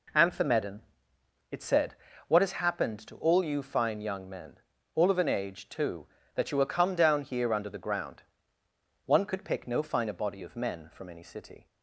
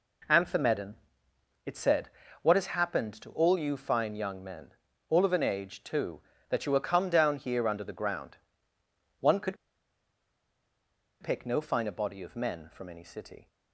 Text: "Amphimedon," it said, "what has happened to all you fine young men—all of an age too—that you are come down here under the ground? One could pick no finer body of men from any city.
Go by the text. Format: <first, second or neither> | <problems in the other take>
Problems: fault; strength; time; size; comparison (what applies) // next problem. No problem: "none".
first | pauses between "could" and "pick"; strong; at 9.5 s; 1.6 s long